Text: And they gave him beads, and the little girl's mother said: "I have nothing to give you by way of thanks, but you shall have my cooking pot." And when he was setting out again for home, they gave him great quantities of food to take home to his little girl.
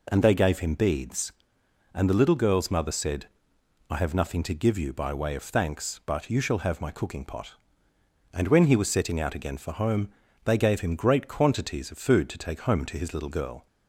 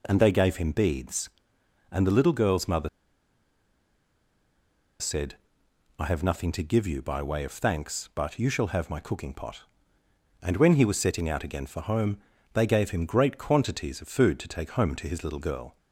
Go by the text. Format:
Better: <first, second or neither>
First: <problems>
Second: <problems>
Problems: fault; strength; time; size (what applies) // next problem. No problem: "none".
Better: first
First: none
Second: pauses between "mother" and "said"; strong; at 2.8 s; 2.1 s long